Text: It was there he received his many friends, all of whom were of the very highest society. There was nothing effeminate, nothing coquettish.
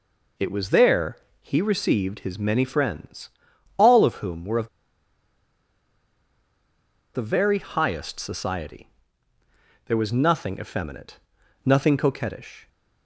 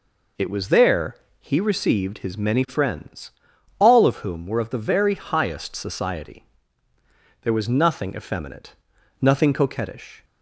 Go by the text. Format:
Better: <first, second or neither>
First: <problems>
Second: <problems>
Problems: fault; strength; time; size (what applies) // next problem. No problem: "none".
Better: second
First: pauses between "there" and "he"; slight; at 1.1 s; 0.24 s long // pauses between "of" and "the"; strong; at 4.6 s; 2.4 s long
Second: pauses between "there" and "he"; slight; at 1.1 s; 0.24 s long